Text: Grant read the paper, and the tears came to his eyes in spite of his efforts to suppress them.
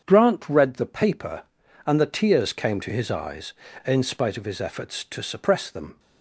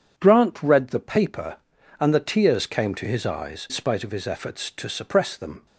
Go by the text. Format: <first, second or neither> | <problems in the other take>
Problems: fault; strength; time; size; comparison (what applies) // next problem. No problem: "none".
first | starts louder than the rest; strong; until 1.1 s; 8 dB; strong in the first // skips "in"; at 3.6 s